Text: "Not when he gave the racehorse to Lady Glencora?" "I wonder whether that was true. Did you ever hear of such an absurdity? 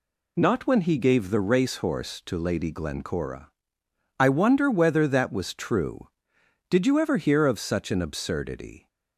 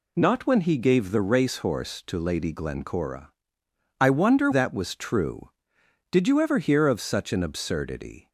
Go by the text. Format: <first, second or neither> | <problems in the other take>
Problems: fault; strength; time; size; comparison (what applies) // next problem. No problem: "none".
first | skips "whether"; at 4.5 s